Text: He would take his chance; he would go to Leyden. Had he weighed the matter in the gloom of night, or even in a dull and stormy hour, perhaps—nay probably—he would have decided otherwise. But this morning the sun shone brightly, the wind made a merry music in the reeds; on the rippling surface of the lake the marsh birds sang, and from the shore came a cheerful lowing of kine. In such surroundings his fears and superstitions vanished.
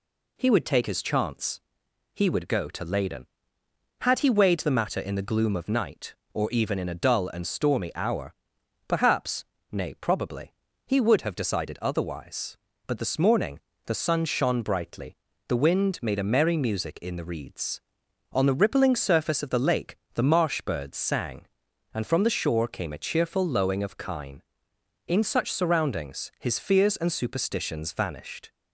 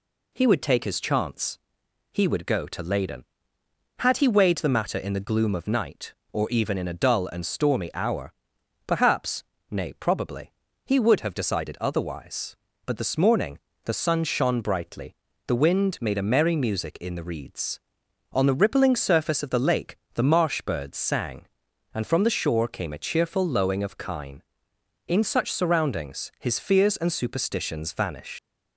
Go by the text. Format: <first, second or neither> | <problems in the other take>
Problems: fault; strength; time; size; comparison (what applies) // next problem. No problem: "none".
first | pauses between "morning" and "the"; slight; at 13.5 s; 0.26 s long; slight in the first // pauses between "lake" and "the"; slight; at 19.9 s; 0.20 s long; slight in the first // leaves "vanished" unfinished; at 28.3 s; 120 ms